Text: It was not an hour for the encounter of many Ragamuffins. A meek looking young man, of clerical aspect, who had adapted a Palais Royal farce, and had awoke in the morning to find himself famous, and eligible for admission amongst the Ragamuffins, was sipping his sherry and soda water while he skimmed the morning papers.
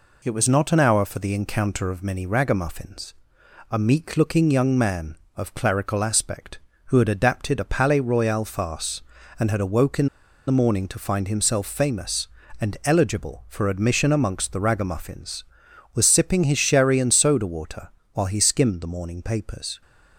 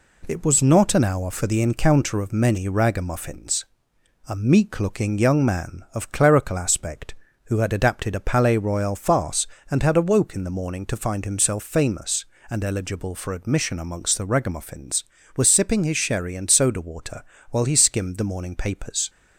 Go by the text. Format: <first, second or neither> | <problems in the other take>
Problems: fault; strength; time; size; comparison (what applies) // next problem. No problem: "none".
second | pauses between "in" and "the"; at 10.0 s; 0.41 s long // pauses between "water" and "while"; slight; at 17.8 s; 0.24 s long; slight in the second